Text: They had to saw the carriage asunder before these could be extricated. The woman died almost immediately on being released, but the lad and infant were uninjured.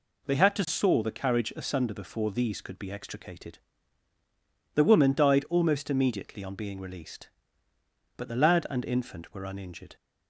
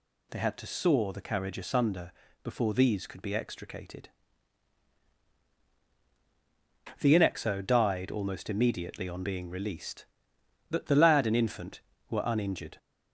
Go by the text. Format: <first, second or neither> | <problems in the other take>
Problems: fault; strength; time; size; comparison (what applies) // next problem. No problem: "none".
first | pauses between "asunder" and "before"; slight; at 2.1 s; 0.32 s long // says "inexo" for "woman"; at 7.1 s